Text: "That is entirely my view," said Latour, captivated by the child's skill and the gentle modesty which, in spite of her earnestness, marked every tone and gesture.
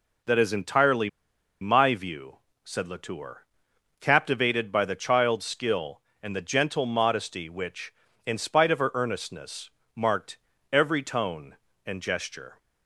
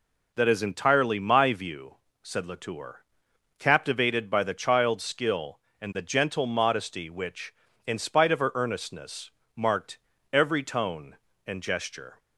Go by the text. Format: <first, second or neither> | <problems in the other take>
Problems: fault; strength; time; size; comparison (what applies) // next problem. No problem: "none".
second | pauses between "entirely" and "my"; noticeable; at 1.0 s; 0.52 s long // pauses between "marked" and "every"; slight; at 10.3 s; 0.34 s long; slight in the second